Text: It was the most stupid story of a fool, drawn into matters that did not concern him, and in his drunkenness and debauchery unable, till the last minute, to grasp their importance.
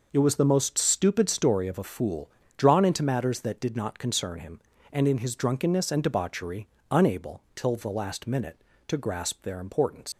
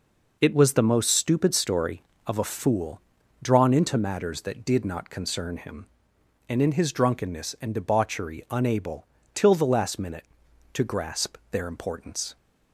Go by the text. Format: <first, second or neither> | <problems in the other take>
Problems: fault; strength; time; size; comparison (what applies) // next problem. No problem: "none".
second | pauses between "debauchery" and "unable"; slight; at 6.6 s; 0.24 s long // leaves "importance" unfinished; at 10.1 s; 95 ms